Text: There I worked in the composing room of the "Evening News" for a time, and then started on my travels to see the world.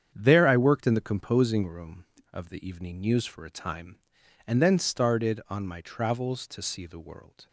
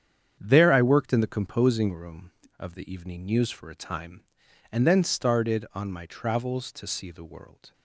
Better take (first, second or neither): neither